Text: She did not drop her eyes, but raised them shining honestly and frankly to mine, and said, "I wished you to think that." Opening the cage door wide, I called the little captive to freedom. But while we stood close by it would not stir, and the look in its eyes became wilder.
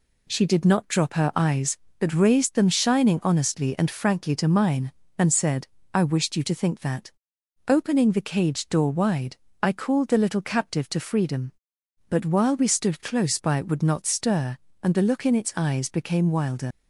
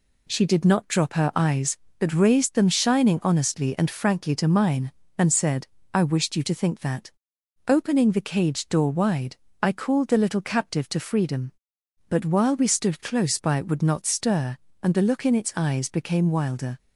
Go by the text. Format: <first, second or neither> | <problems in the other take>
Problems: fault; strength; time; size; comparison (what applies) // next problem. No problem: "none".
second | leaves "wilder" unfinished; at 16.7 s; 70 ms